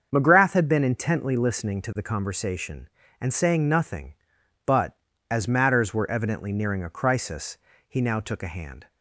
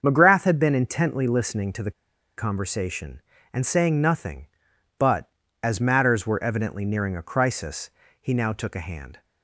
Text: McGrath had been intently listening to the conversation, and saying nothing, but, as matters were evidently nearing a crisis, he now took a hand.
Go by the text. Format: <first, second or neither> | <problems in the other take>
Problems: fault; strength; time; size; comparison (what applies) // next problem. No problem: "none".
first | starts louder than the rest; until 1.0 s; 7 dB; also in the first // pauses between "the" and "conversation"; noticeable; at 1.9 s; 0.47 s long